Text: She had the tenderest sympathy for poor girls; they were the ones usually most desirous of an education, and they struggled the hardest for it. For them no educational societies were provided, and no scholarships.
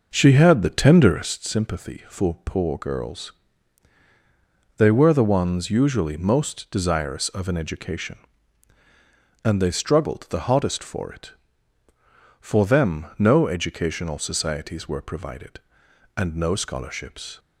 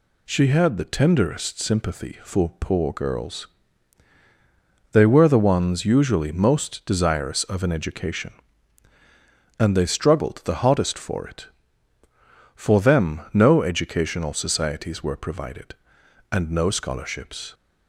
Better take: second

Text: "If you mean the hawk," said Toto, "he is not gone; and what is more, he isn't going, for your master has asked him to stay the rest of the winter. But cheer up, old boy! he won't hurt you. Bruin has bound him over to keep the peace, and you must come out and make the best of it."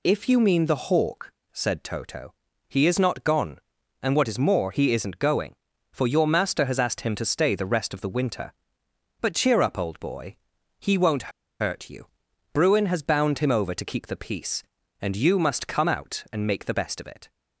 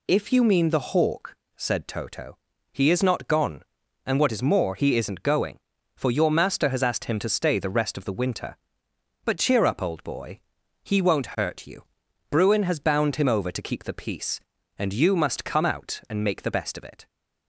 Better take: second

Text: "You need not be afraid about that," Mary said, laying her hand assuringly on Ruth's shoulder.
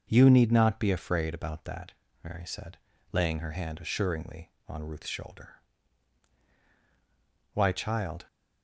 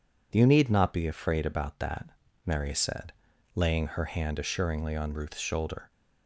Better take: second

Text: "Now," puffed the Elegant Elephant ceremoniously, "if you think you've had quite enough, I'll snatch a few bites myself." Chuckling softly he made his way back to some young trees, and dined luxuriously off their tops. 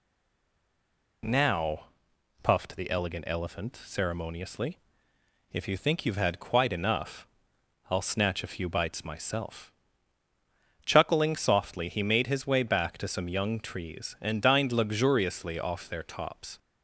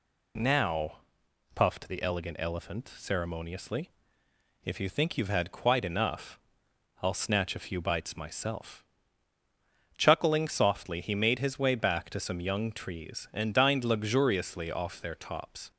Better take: second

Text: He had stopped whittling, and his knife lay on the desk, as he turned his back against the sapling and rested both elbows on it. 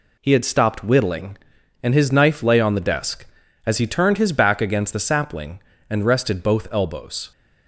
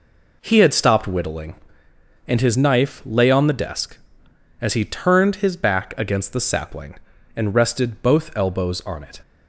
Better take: second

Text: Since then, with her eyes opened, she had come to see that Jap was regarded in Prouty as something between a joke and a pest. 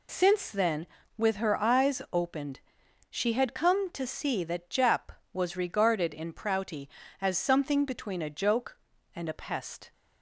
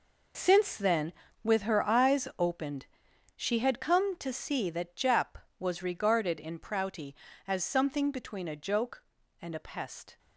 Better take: first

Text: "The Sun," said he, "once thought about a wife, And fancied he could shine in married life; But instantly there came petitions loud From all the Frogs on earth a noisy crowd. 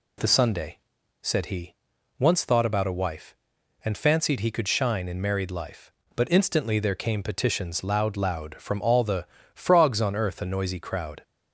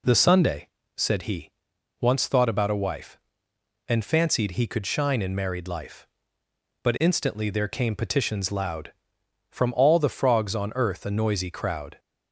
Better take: second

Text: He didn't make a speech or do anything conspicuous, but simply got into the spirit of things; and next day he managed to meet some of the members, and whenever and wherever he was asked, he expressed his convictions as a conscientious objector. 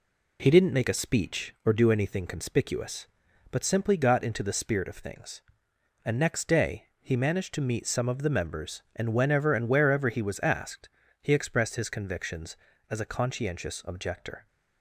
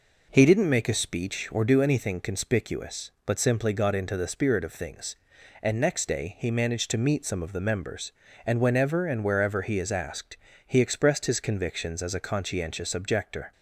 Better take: first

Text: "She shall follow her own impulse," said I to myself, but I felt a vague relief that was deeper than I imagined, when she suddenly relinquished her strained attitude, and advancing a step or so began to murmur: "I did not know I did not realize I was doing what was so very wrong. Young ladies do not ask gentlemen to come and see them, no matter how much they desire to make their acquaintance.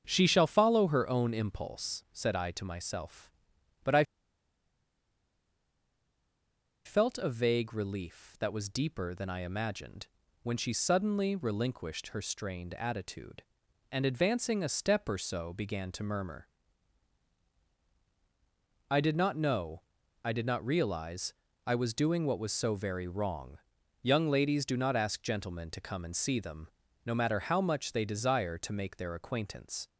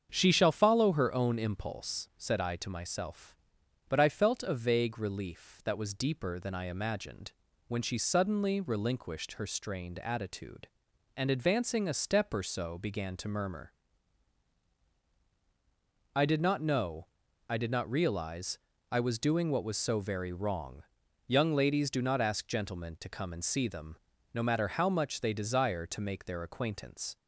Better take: second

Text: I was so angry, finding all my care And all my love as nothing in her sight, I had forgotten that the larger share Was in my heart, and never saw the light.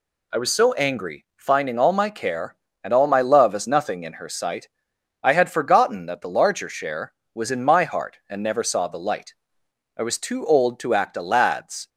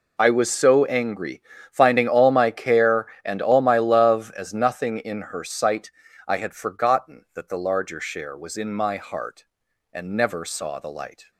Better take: second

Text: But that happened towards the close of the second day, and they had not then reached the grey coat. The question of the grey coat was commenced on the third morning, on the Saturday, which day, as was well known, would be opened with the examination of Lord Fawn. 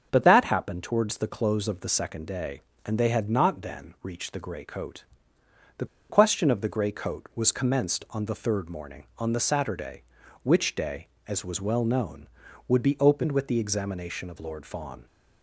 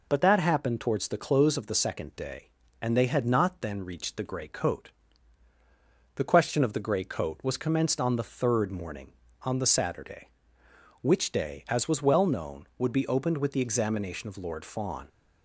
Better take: second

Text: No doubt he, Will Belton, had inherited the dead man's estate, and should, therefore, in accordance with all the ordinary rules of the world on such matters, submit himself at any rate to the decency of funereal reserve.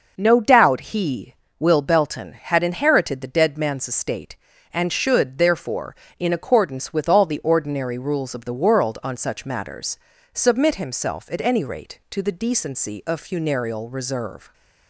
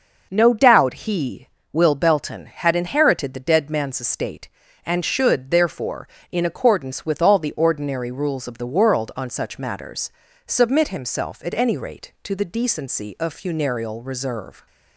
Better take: neither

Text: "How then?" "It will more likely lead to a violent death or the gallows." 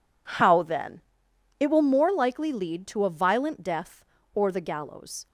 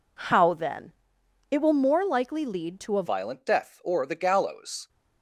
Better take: first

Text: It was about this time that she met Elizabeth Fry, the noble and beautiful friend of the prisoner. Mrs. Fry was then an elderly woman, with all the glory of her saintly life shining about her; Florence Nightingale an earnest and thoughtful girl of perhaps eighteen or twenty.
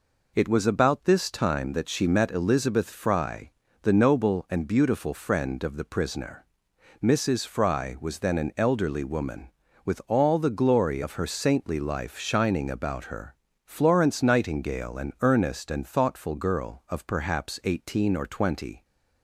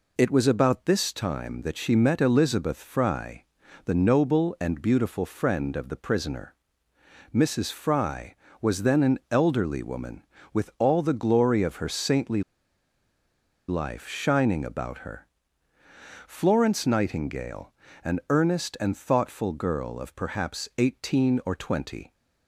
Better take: first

